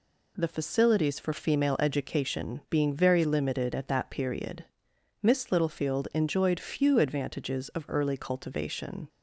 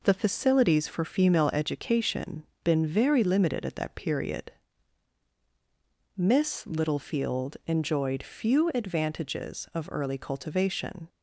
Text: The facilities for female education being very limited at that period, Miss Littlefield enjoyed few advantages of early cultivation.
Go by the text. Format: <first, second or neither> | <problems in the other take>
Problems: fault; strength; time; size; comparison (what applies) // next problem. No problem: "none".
first | says "been" for "being"; at 2.6 s